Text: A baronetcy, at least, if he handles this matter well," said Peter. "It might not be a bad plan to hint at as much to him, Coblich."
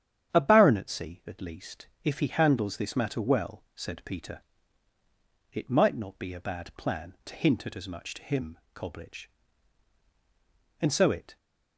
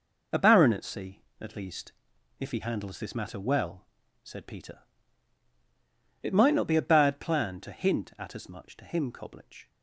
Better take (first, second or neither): second